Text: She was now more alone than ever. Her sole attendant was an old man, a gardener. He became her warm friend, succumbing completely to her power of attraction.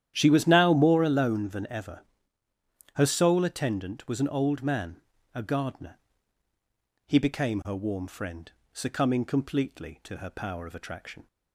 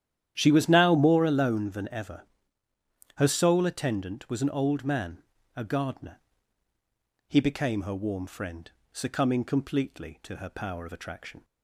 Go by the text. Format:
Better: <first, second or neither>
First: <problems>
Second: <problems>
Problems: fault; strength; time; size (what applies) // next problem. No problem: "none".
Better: neither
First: starts louder than the rest; strong; until 1.1 s; 10.5 dB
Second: starts louder than the rest; strong; until 1.3 s; 10.5 dB